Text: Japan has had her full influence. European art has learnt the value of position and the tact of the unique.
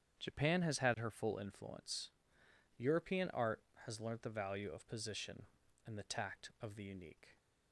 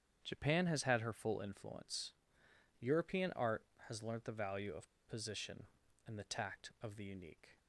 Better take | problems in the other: first | starts louder than the rest; strong; until 1.2 s; 8.5 dB; strong in the first // pauses between "of" and "position"; slight; at 4.8 s; 0.19 s long

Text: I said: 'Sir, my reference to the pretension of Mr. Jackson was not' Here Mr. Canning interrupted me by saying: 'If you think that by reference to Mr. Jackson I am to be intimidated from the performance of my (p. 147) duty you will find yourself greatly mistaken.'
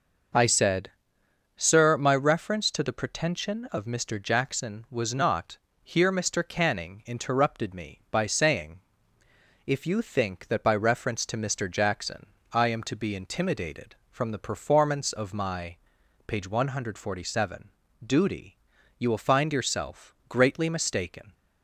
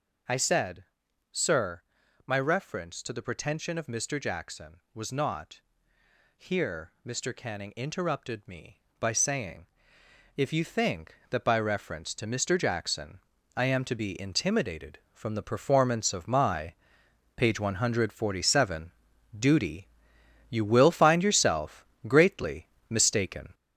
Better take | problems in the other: first | gets louder; noticeable; throughout; 5.5 dB // pauses between "not" and "Here"; noticeable; at 5.5 s; 0.76 s long; slight in the first // pauses between "Jackson" and "I"; slight; at 13.1 s; 0.36 s long; slight in the first // pauses between "duty" and "you"; noticeable; at 19.8 s; 0.64 s long; also in the first // pauses between "yourself" and "greatly"; slight; at 21.8 s; 0.18 s long // pauses between "greatly" and "mistaken"; slight; at 22.6 s; 0.24 s long

